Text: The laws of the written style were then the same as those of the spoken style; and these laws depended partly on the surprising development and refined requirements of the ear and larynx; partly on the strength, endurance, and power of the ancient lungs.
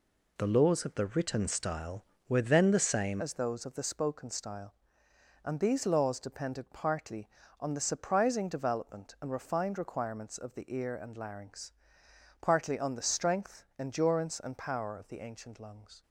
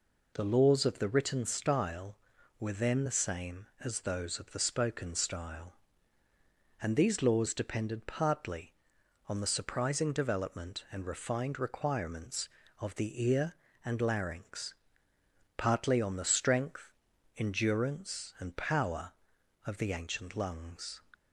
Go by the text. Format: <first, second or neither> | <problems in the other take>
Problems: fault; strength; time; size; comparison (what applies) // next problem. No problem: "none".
second | changes voice at "as"; from 3.1 s on; 12.9 s long